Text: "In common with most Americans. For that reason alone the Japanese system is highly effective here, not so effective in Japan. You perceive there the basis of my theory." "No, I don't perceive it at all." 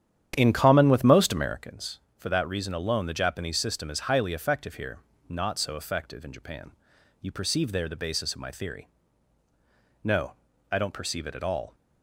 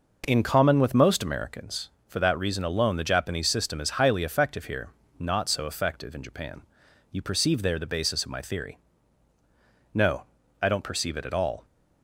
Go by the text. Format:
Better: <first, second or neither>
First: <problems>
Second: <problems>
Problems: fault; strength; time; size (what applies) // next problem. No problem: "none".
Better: second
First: starts louder than the rest; strong; until 1.6 s; 9.5 dB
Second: none